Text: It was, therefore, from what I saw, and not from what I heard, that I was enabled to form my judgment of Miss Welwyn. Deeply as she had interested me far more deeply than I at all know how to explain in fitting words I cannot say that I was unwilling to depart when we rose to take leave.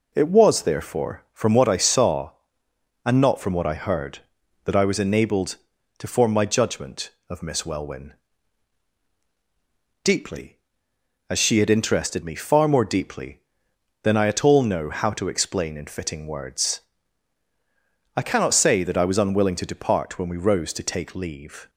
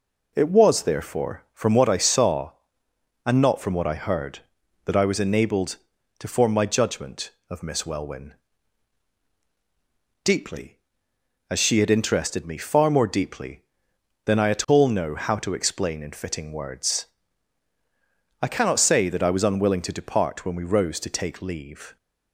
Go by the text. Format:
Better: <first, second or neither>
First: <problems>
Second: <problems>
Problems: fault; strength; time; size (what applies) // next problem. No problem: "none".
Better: neither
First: pauses between "words" and "I"; strong; at 16.8 s; 1.3 s long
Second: pauses between "words" and "I"; strong; at 17.0 s; 1.3 s long